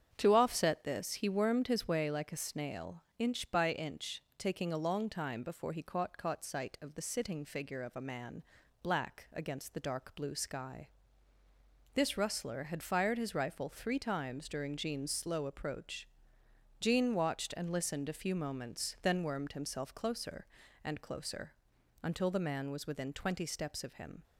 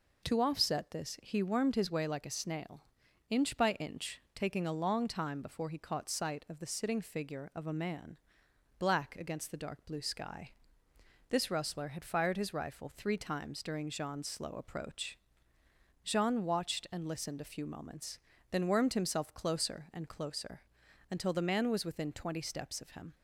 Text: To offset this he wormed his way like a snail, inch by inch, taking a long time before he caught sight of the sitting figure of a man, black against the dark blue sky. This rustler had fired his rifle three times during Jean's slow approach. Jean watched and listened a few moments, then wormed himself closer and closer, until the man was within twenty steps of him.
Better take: second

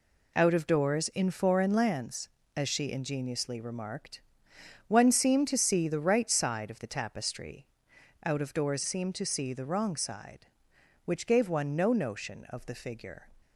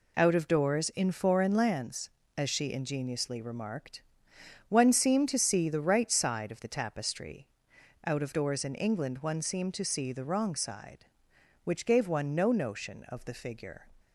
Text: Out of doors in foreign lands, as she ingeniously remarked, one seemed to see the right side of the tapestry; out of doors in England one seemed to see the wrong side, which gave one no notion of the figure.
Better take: second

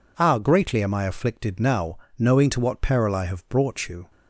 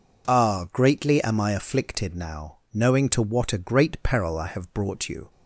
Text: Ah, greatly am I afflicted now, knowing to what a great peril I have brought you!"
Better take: second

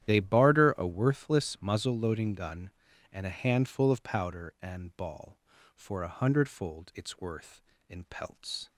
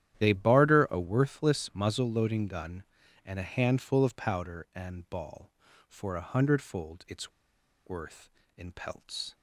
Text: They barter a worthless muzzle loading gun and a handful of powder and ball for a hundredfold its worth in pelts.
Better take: first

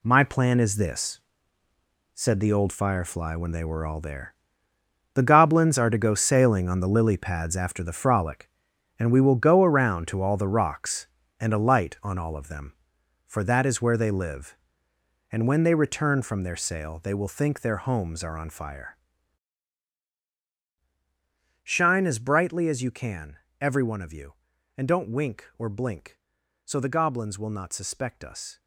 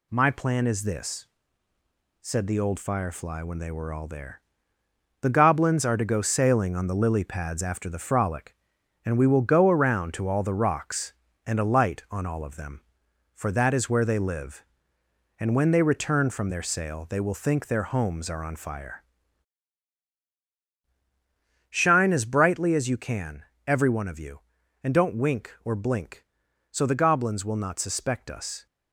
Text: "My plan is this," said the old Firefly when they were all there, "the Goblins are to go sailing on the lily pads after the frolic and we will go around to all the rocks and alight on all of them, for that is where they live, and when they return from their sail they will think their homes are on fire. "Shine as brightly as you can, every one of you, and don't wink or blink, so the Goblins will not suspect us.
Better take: second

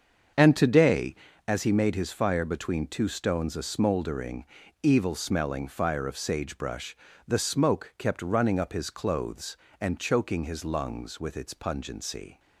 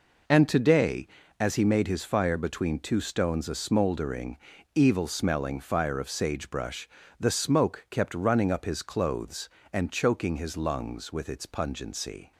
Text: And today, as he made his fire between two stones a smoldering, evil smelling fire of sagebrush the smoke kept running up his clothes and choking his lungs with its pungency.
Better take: second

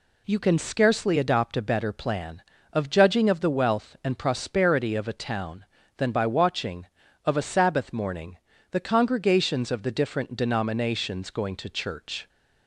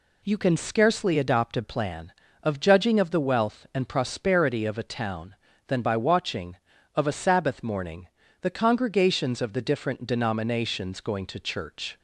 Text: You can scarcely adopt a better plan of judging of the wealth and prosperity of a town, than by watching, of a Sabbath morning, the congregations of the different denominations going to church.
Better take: first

